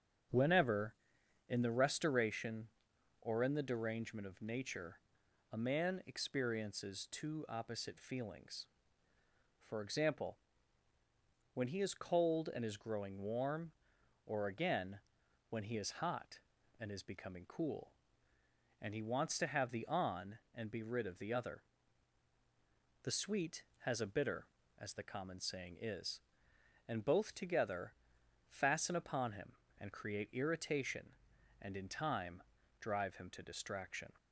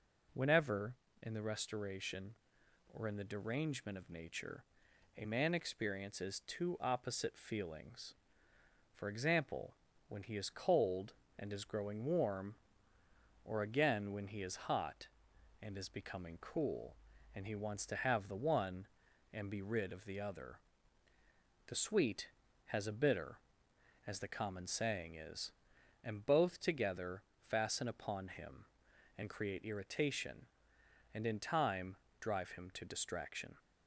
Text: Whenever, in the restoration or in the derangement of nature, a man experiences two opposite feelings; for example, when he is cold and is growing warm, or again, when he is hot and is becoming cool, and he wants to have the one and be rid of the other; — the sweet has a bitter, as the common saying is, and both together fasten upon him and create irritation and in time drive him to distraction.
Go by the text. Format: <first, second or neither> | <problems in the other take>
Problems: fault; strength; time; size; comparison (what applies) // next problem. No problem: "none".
second | starts louder than the rest; strong; until 1.8 s; 8.5 dB // says "on" for "one"; at 19.8 s // pauses between "together" and "fasten"; noticeable; at 27.9 s; 0.52 s long; slight in the second // pauses between "time" and "drive"; at 32.4 s; 0.38 s long; slight in the second